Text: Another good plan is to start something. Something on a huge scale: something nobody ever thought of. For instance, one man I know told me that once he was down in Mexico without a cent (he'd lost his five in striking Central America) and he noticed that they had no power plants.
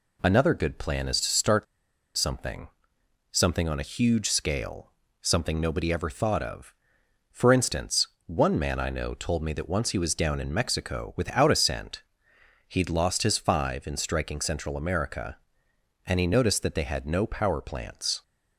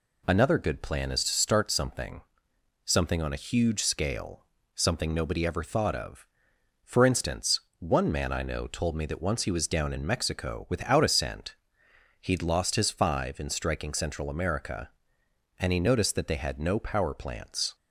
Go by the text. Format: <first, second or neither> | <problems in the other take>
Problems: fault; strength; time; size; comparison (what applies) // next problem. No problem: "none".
second | pauses between "start" and "something"; noticeable; at 1.6 s; 0.51 s long